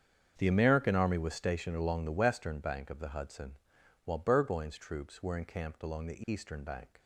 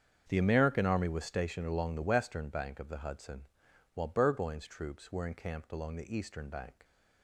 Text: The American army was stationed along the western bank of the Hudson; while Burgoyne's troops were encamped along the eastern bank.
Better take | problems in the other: neither | starts louder than the rest; strong; the same in both

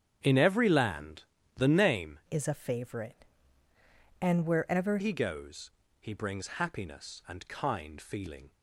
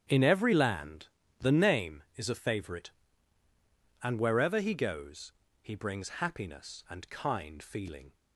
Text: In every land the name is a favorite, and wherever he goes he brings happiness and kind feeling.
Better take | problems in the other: second | starts louder than the rest; strong; until 1.2 s; 8.5 dB; strong in the second // pauses between "land" and "the"; slight; at 1.2 s; 0.32 s long; slight in the second // changes voice from "is" to "wherever"; from 2.2 to 4.9 s; 2.7 s long // pauses between "goes" and "he"; slight; at 5.7 s; 0.30 s long; slight in the second

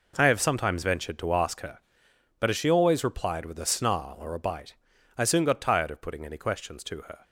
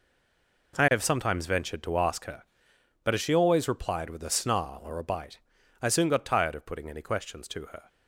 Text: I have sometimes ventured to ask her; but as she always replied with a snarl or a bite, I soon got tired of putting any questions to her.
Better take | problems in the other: first | stays silent before the first word; slight; until 0.7 s; 0.7 s long

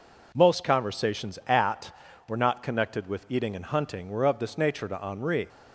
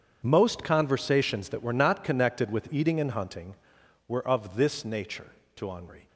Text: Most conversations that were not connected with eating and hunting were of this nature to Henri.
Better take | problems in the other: second | says "at" for "that"; at 1.4 s

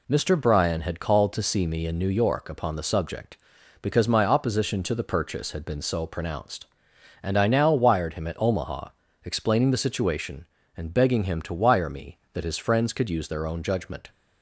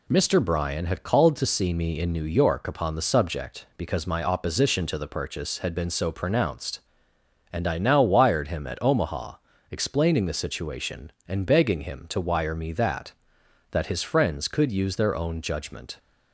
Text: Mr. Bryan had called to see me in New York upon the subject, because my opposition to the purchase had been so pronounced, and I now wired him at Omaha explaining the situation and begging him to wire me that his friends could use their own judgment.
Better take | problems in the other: first | pauses between "Omaha" and "explaining"; slight; at 9.3 s; 0.36 s long; also in the first // says "that" twice; at 13.7 s

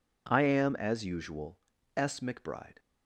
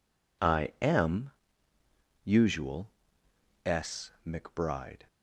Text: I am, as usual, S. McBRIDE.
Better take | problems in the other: first | skips "as"; at 1.7 s

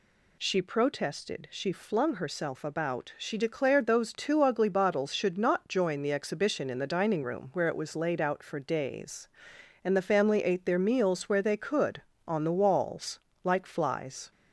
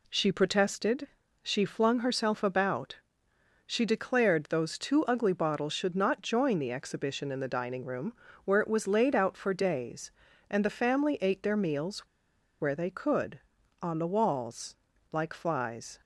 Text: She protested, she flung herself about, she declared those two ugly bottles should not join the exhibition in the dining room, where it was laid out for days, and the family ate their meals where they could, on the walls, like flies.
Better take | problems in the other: first | pauses between "meals" and "where"; noticeable; at 12.0 s; 0.56 s long

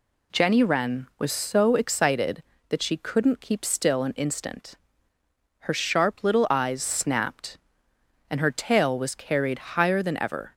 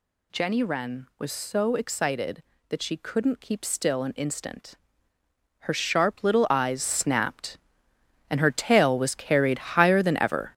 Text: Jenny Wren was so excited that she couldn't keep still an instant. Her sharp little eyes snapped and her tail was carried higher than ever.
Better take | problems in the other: first | gets louder; strong; throughout; 7.5 dB

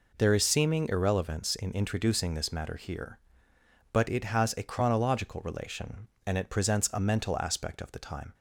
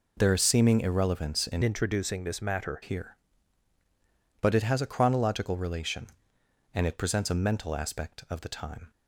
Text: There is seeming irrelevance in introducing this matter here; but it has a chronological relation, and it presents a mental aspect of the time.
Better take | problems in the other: first | changes voice from "introducing" to "matter"; from 1.6 to 2.8 s; 1.2 s long

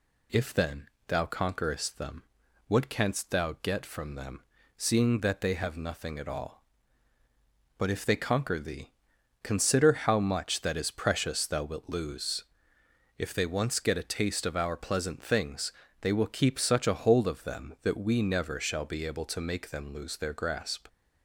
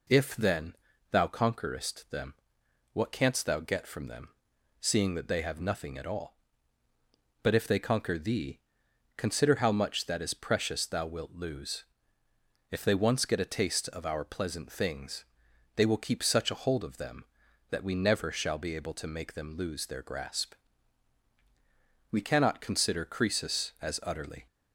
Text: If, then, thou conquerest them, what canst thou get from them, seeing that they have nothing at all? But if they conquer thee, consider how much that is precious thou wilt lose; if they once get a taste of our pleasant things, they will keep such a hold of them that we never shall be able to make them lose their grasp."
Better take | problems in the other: first | goes on to say "We cannot consider Croesus as utterly"; strong; from 22.1 s on; 2.3 s long

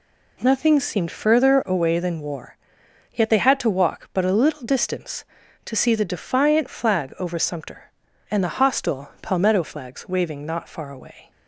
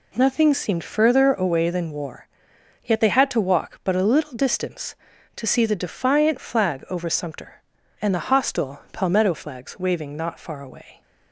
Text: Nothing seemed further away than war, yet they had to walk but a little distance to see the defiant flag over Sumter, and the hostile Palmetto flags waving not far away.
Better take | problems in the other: neither | none

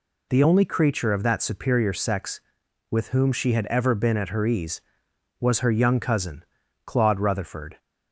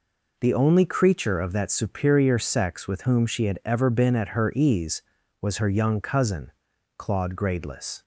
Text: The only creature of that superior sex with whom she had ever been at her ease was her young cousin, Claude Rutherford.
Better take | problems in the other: first | says "Gradeless" for "Rutherford"; at 7.3 s

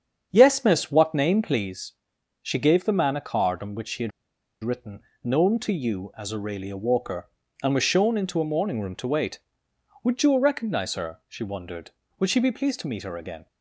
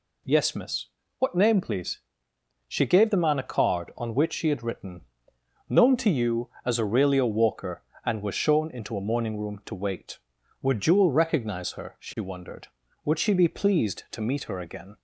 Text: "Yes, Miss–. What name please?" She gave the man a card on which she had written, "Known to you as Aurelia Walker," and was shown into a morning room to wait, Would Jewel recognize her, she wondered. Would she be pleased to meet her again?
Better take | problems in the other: second | starts louder than the rest; strong; until 1.3 s; 7.5 dB // pauses between "had" and "written"; noticeable; at 4.1 s; 0.51 s long

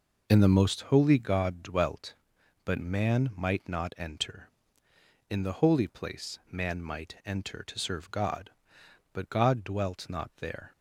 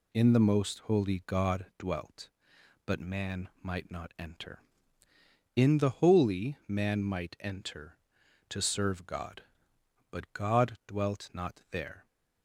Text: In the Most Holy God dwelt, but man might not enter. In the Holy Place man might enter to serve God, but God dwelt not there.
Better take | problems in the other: first | skips "Place"; at 6.6 s

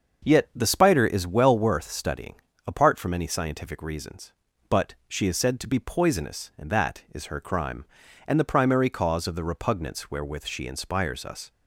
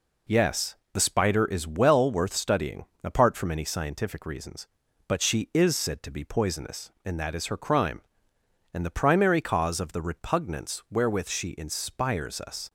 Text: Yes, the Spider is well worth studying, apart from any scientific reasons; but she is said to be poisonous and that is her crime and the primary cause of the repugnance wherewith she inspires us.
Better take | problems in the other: second | starts louder than the rest; until 1.3 s; 6.5 dB // says "Yet" for "Yes"; at 0.2 s // pauses between "but" and "she"; slight; at 4.9 s; 0.16 s long

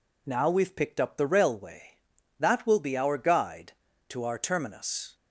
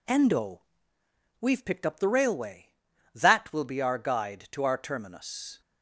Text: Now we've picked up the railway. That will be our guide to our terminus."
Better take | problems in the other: first | says "Endo" for "Now"; at 0.0 s

